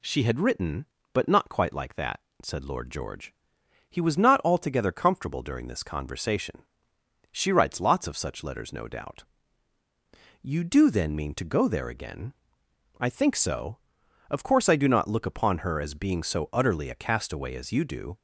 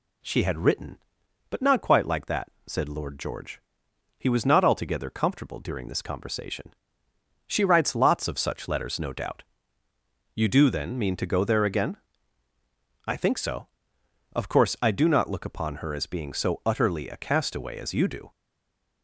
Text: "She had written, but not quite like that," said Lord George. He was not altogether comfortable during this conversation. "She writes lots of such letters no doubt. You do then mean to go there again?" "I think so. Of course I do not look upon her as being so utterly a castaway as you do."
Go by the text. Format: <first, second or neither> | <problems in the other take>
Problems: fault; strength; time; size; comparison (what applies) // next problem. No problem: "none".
first | stays silent after the last word; slight; from 18.2 s on; 0.8 s long